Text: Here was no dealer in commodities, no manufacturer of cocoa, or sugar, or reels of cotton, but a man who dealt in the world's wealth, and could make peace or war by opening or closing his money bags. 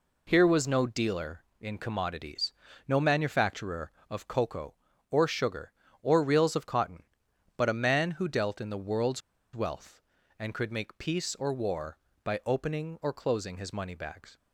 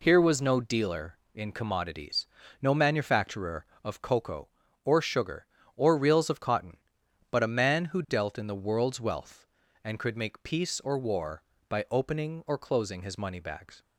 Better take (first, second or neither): second